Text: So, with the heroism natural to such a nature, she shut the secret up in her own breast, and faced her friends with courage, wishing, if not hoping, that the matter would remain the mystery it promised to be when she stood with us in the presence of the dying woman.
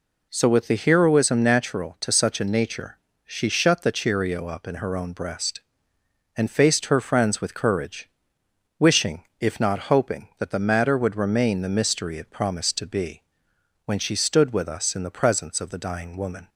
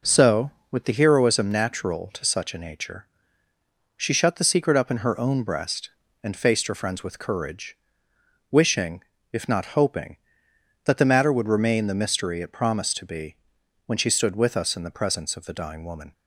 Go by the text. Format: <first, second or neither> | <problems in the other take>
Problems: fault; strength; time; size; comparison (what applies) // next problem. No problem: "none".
second | says "cheerio" for "secret"; at 3.9 s // pauses between "be" and "when"; noticeable; at 13.2 s; 0.64 s long; noticeable in the second